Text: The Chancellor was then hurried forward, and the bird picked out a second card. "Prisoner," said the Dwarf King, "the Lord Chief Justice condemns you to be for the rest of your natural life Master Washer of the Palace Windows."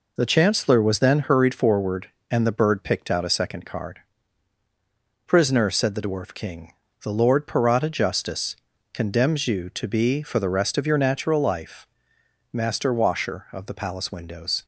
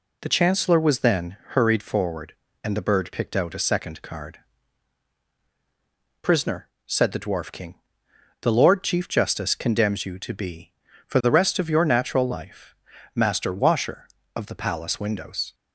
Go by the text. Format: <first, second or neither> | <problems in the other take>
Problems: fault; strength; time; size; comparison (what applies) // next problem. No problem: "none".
second | says "Parata" for "Chief"; at 7.4 s // pauses between "Justice" and "condemns"; at 8.5 s; 0.38 s long // pauses between "life" and "Master"; noticeable; at 11.8 s; 0.66 s long; also in the second